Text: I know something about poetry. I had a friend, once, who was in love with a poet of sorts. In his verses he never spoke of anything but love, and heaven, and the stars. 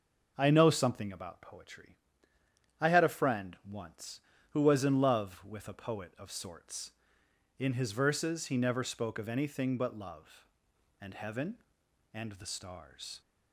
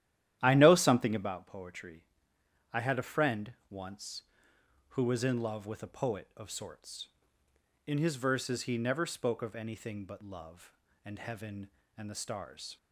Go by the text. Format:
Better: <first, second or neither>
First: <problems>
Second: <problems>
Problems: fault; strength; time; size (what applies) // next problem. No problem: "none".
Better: first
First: none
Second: starts louder than the rest; strong; until 1.3 s; 12 dB